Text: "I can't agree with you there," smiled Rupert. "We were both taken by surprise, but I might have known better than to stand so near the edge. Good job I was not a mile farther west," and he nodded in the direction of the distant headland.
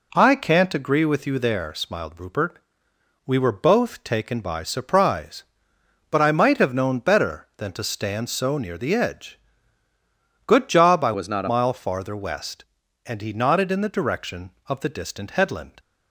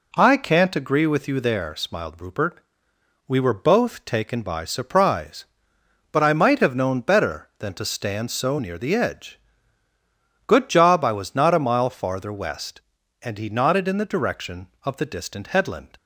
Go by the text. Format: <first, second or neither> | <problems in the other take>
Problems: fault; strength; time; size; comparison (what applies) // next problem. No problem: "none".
second | changes voice from "was" to "a"; from 11.1 to 11.4 s; 0.3 s long